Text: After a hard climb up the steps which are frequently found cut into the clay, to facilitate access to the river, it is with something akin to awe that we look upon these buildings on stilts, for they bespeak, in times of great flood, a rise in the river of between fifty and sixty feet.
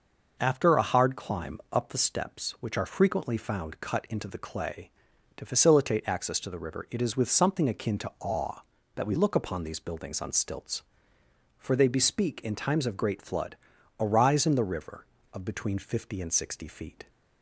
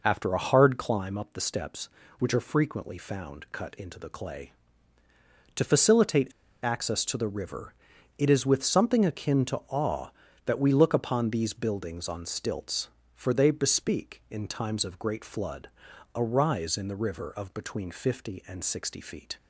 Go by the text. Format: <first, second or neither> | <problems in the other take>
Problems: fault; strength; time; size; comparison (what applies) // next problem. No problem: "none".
first | pauses between "facilitate" and "access"; slight; at 6.3 s; 0.32 s long